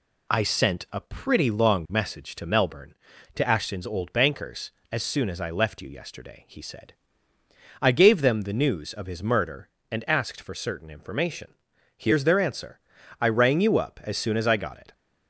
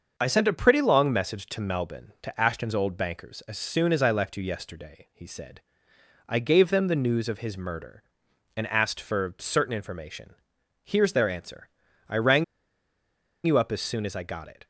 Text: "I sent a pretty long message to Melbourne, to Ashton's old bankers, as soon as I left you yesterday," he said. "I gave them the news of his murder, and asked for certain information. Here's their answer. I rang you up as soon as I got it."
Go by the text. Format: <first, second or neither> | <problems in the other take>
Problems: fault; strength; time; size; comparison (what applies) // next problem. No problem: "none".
first | starts louder than the rest; until 1.1 s; 6 dB // pauses between "rang" and "you"; at 12.4 s; 1.0 s long